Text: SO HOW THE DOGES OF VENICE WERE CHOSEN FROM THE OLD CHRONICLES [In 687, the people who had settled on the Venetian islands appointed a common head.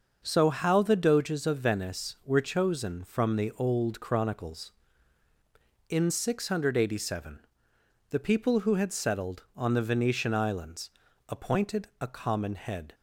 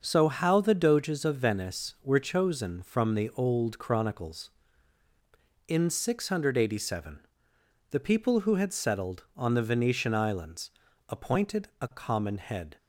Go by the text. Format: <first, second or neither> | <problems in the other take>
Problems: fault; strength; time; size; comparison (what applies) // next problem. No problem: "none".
neither | starts louder than the rest; the same in both // pauses between "islands" and "appointed"; slight; the same in both